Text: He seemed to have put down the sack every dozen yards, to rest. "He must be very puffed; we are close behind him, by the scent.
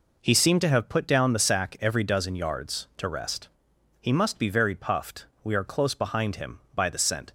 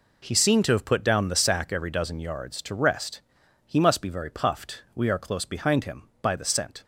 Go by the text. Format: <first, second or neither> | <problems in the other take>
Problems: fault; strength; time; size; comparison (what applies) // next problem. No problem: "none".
neither | none